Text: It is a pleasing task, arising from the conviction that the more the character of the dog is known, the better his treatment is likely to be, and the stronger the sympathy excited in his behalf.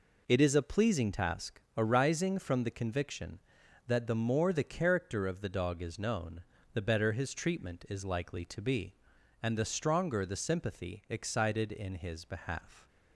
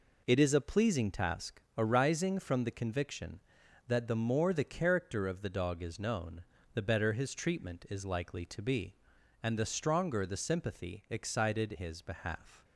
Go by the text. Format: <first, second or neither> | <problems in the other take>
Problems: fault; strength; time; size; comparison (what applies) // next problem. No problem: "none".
first | skips "in"; at 11.7 s